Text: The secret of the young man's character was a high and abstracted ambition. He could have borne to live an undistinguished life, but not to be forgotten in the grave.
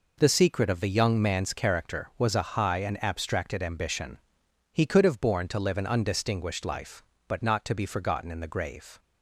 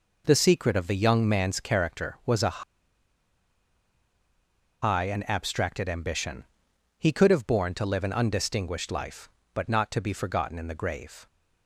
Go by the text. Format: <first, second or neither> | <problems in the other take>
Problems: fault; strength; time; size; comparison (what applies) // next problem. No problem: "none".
first | pauses between "a" and "high"; strong; at 2.6 s; 2.2 s long